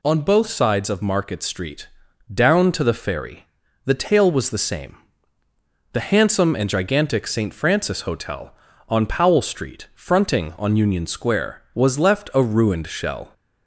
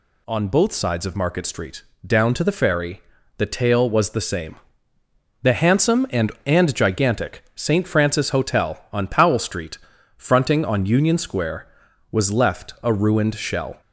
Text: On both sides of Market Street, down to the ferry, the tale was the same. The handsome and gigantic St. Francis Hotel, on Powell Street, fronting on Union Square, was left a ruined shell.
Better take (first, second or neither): first